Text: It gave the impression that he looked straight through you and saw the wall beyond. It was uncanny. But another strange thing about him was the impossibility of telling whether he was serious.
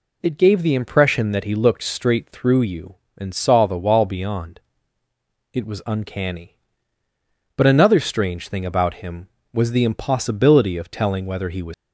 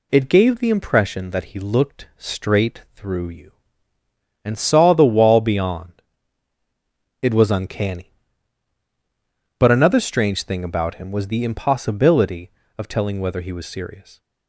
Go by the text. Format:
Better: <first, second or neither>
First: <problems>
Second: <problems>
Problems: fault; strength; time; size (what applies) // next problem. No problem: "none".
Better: second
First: stops before "serious"; at 11.7 s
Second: none